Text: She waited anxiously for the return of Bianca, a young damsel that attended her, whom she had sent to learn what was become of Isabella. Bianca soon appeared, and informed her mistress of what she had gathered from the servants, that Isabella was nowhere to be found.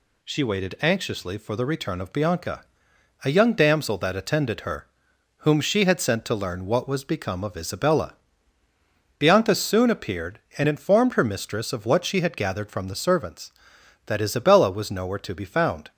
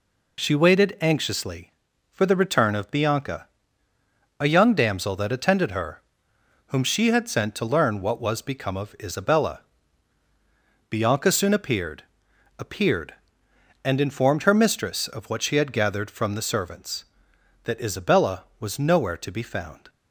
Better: first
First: none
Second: says "appeared" twice; at 12.5 s

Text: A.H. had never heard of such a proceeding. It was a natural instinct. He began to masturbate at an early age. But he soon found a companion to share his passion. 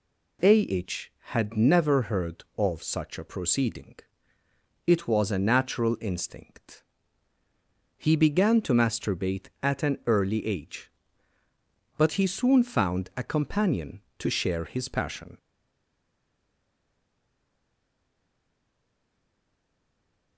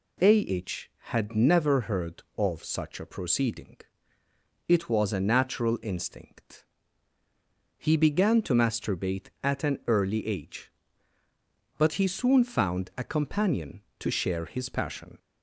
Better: second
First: stays silent after the last word; strong; from 15.3 s on; 5.0 s long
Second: none

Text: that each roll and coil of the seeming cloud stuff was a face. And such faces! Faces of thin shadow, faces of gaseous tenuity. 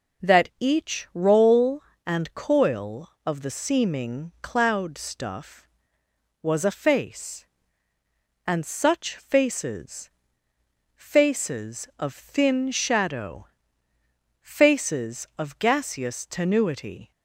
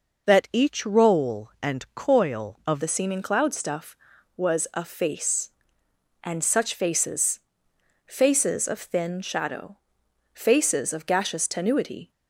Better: first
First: none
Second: changes voice at "the"; from 2.8 s on; 9.3 s long

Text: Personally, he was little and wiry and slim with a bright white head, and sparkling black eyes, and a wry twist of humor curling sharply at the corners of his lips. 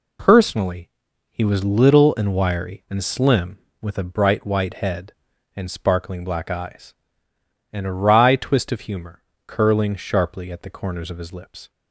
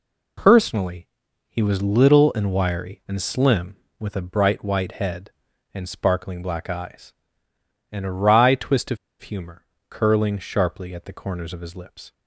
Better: first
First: pauses between "humor" and "curling"; slight; at 9.2 s; 0.24 s long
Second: pauses between "of" and "humor"; slight; at 8.9 s; 0.25 s long // pauses between "humor" and "curling"; slight; at 9.6 s; 0.24 s long

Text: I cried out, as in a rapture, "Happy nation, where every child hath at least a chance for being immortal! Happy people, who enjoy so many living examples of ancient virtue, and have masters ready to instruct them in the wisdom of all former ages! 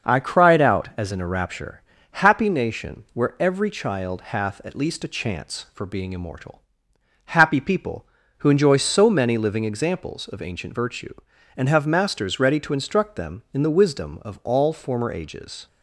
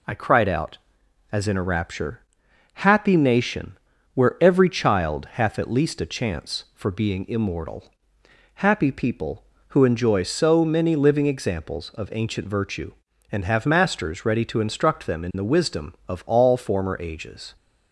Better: second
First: starts louder than the rest; noticeable; until 1.0 s; 6 dB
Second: none

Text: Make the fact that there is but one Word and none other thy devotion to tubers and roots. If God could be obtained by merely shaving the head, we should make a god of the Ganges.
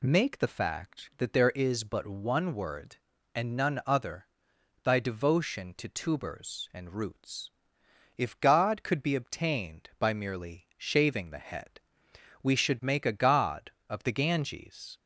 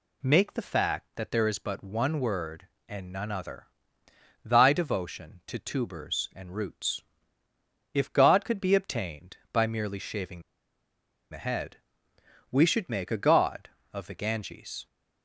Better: first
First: pauses between "other" and "thy"; noticeable; at 4.2 s; 0.56 s long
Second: pauses between "other" and "thy"; noticeable; at 3.6 s; 0.76 s long // pauses between "shaving" and "the"; noticeable; at 10.4 s; 0.89 s long

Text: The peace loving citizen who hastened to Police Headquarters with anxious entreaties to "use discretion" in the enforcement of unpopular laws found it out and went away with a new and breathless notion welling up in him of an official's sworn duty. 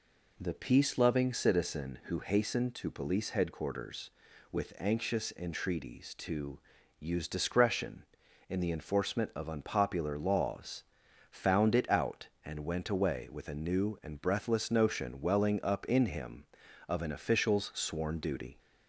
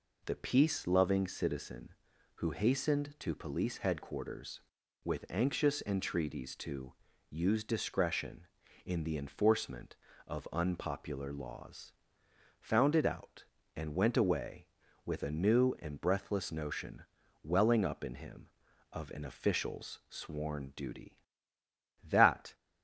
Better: first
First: pauses between "to" and "use"; at 6.5 s; 0.40 s long // pauses between "laws" and "found"; noticeable; at 10.8 s; 0.46 s long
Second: pauses between "to" and "use"; slight; at 6.9 s; 0.36 s long // pauses between "laws" and "found"; noticeable; at 11.9 s; 0.70 s long // pauses between "notion" and "welling"; at 17.0 s; 0.40 s long // goes on to say "That"; from 22.0 s on; 0.54 s long

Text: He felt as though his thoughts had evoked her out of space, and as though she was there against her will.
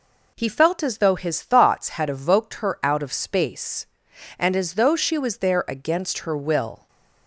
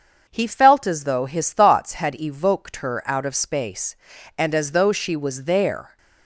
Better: first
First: none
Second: starts louder than the rest; until 1.2 s; 6.5 dB // stops before "against her will"; at 5.9 s

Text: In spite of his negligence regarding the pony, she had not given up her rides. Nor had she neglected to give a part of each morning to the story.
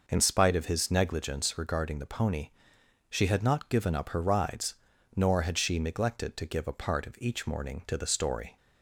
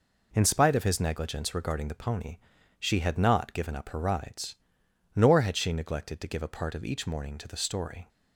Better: neither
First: none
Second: none

